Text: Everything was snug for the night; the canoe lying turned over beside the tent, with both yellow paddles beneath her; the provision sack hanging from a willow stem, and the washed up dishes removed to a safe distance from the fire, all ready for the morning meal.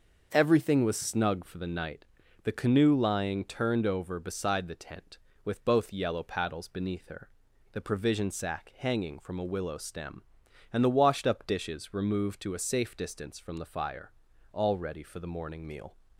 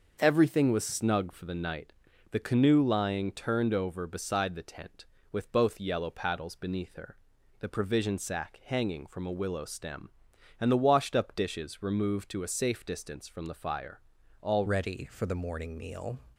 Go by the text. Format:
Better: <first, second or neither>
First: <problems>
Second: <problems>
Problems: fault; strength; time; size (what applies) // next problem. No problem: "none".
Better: first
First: starts louder than the rest; until 1.3 s; 6.5 dB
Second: starts louder than the rest; until 1.2 s; 6.5 dB // changes voice at "ready"; from 14.6 s on; 1.5 s long